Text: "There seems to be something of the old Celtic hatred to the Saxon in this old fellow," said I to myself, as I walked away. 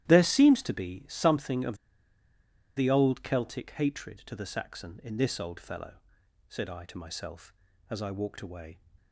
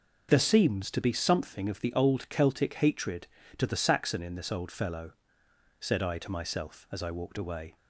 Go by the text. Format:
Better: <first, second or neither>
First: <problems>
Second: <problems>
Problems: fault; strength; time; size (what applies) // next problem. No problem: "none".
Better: second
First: starts louder than the rest; strong; until 1.1 s; 12.5 dB // pauses between "of" and "the"; at 1.7 s; 1.0 s long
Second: none